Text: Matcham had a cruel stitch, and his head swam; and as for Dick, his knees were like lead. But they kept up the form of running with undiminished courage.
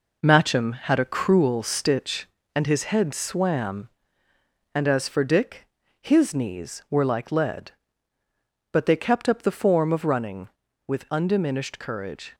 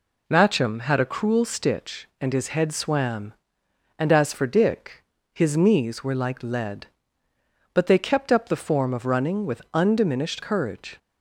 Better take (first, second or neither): second